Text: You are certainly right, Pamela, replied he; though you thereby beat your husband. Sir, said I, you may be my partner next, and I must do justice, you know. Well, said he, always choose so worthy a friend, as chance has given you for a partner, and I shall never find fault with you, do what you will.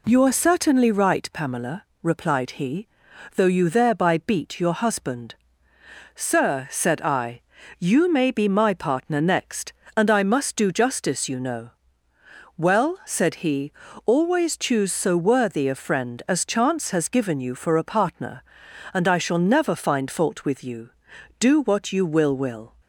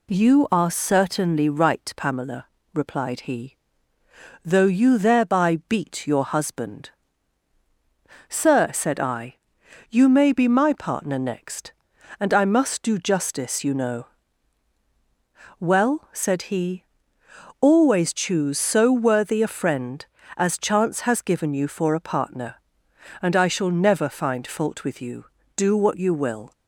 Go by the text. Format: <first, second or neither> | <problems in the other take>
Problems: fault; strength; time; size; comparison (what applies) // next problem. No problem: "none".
second | says "will" twice; at 22.3 s